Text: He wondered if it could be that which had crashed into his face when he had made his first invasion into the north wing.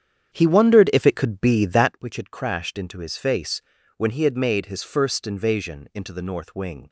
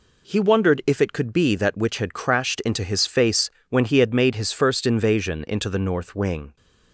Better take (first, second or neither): second